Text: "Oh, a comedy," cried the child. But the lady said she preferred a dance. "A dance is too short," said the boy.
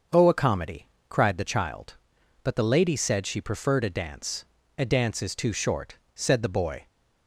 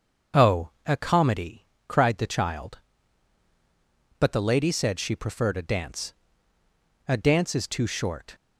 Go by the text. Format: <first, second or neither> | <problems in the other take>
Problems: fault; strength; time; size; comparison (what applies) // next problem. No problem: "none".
first | starts louder than the rest; until 1.5 s; 6.5 dB; also in the first // stops before "said the boy"; at 8.3 s